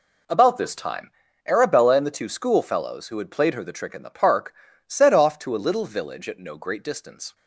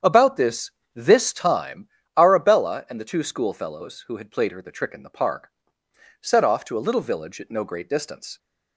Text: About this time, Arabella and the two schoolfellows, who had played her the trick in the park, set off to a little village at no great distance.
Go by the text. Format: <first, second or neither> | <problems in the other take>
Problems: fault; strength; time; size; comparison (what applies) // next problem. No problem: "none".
first | starts louder than the rest; strong; until 1.2 s; 8 dB // says "this" twice; at 0.9 s